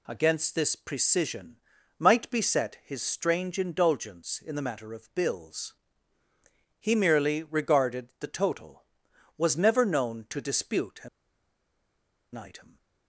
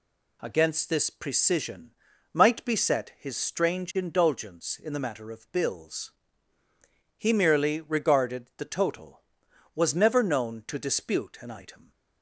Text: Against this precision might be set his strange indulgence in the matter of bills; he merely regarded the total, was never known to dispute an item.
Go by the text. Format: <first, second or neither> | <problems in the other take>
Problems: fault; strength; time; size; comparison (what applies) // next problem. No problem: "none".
second | pauses between "precision" and "might"; at 1.5 s; 0.40 s long; also in the second // pauses between "an" and "item"; strong; at 11.0 s; 1.2 s long